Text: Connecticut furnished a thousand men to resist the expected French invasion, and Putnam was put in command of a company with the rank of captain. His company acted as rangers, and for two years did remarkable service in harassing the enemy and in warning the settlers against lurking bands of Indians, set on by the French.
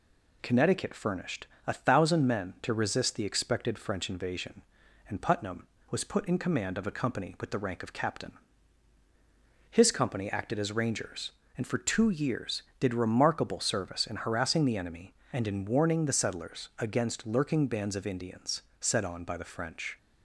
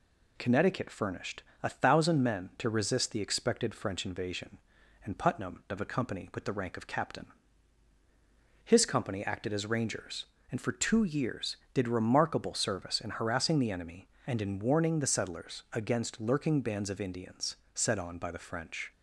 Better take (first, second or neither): first